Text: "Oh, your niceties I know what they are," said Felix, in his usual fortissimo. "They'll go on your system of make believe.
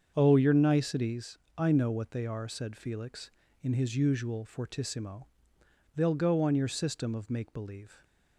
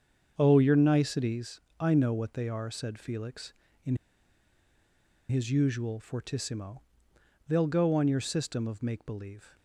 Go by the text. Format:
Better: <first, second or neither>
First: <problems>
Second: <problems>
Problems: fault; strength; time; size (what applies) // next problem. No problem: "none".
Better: first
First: starts louder than the rest; strong; until 1.1 s; 7 dB // pauses between "niceties" and "I"; slight; at 1.3 s; 0.18 s long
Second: starts louder than the rest; strong; until 1.3 s; 7 dB // pauses between "niceties" and "I"; slight; at 1.6 s; 0.18 s long // pauses between "in" and "his"; strong; at 3.9 s; 1.3 s long